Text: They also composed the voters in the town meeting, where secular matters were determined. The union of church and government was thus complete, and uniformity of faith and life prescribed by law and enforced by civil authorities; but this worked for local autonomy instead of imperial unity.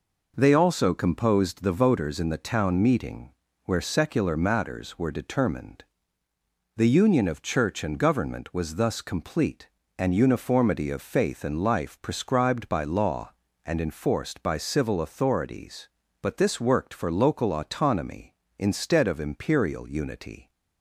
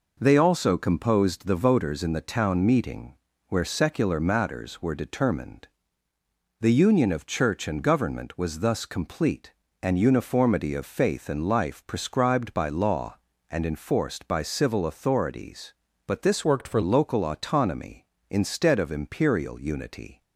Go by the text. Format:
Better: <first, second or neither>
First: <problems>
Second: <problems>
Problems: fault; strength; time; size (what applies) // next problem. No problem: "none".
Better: first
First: none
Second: changes voice from "worked" to "for"; from 16.4 to 16.8 s; 0.4 s long